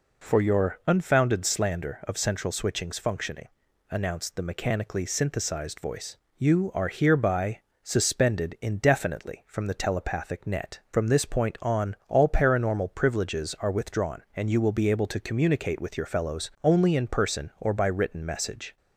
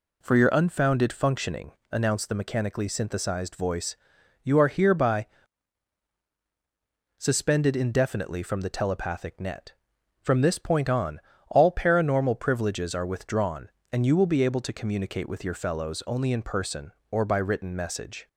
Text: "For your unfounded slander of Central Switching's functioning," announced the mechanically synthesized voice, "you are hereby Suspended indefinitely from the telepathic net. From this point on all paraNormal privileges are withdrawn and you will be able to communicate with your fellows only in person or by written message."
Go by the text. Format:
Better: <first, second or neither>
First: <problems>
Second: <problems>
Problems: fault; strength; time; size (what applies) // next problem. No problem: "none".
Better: first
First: pauses between "hereby" and "Suspended"; slight; at 7.5 s; 0.24 s long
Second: skips "slander of Central Switching's"; at 1.1 s // pauses between "hereby" and "Suspended"; strong; at 5.2 s; 1.9 s long // pauses between "on" and "all"; slight; at 11.1 s; 0.30 s long